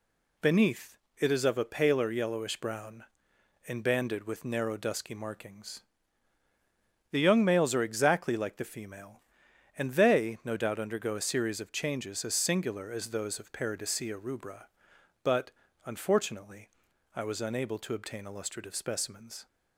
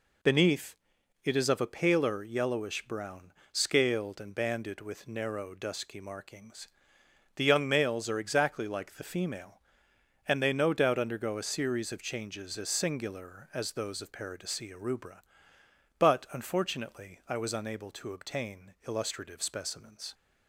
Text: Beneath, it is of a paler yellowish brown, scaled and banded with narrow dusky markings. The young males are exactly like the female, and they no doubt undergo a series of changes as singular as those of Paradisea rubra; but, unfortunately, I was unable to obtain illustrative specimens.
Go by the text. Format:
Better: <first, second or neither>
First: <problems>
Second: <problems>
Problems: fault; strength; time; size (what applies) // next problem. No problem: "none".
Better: second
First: skips "scaled"; at 3.3 s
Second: none